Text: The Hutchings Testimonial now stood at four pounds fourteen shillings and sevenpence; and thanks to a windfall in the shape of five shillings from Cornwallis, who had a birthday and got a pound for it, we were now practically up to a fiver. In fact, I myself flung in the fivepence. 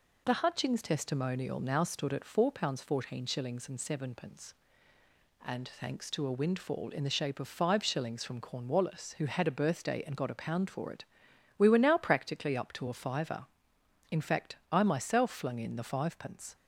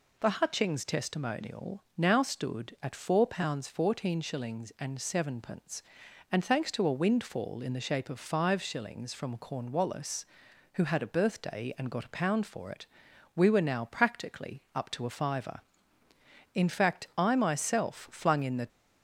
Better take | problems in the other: first | stops before "fivepence"; at 18.6 s

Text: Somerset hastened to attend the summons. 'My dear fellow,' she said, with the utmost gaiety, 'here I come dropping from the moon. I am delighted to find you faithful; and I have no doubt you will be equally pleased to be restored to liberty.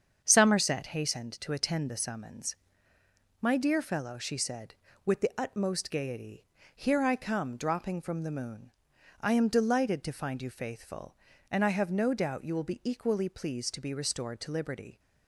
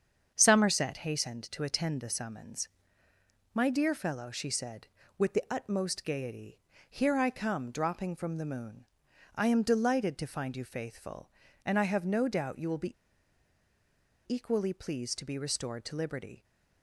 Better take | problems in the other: first | starts louder than the rest; strong; until 1.3 s; 7.5 dB; strong in the first // pauses between "be" and "equally"; strong; at 12.9 s; 1.3 s long

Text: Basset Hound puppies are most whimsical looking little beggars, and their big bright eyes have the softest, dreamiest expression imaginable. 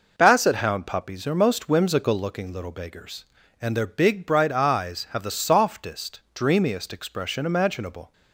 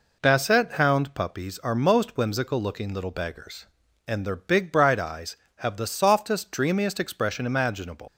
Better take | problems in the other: first | leaves "imaginable" unfinished; at 8.0 s; 125 ms

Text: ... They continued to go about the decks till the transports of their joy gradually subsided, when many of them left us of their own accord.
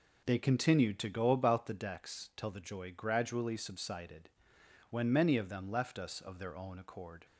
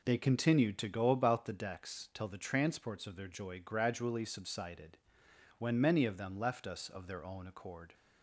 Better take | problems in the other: second | skips "transports of their"; at 2.6 s

